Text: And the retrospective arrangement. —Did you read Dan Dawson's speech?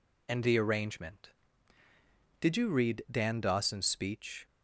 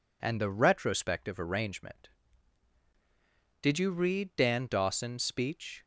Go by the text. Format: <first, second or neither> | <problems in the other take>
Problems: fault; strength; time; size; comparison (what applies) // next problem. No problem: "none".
second | skips "retrospective"; at 0.5 s